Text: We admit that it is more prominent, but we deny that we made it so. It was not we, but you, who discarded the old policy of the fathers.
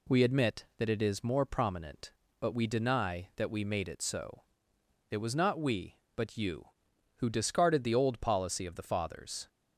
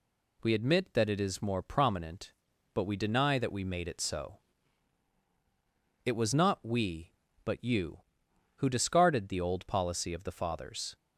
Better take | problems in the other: neither | none

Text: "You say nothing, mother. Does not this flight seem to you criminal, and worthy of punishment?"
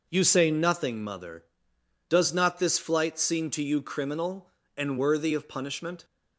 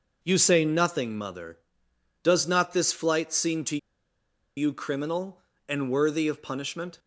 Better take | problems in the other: first | pauses between "to" and "you"; noticeable; at 3.7 s; 0.79 s long

